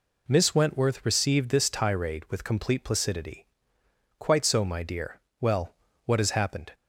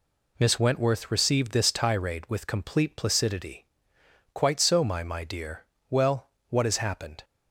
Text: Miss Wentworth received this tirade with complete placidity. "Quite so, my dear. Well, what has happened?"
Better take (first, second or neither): first